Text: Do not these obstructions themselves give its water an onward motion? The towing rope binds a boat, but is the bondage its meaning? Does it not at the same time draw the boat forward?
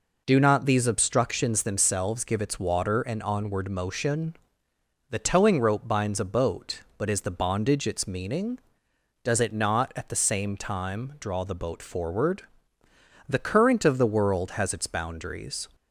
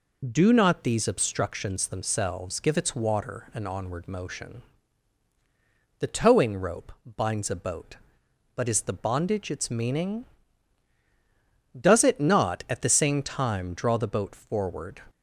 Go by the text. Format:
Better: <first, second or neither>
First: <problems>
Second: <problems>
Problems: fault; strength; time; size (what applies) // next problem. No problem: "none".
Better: second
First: goes on to say "The current of the world has its boundaries"; strong; from 13.2 s on; 2.4 s long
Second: none